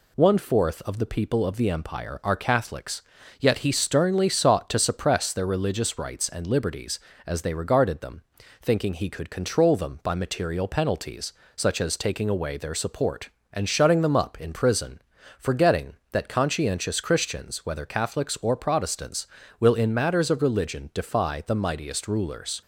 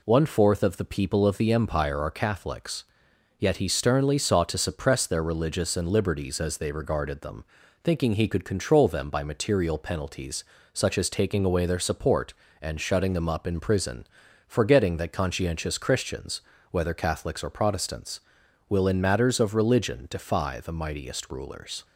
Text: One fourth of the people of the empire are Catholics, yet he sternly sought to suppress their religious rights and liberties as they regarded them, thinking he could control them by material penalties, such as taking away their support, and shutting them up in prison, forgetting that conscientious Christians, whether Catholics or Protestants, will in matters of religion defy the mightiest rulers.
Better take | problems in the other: first | skips "rights"; at 5.7 s

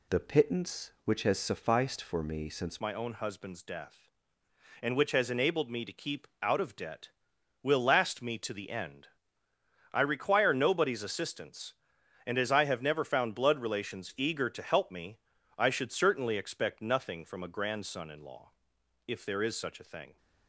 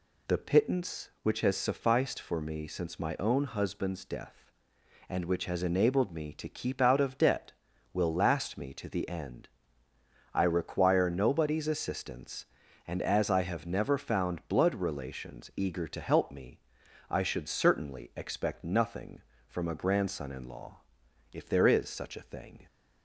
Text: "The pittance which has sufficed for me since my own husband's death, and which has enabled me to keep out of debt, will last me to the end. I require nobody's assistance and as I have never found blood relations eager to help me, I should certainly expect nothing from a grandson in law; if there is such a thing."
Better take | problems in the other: second | changes voice at "my"; from 2.8 s on; 17.3 s long // pauses between "keep" and "out"; slight; at 6.2 s; 0.16 s long

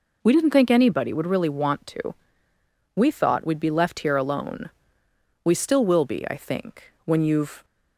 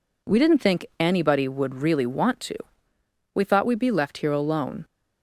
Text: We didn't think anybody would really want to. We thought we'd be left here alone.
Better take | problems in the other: second | goes on to say "We still will be I think when you've"; strong; from 5.4 s on; 2.2 s long

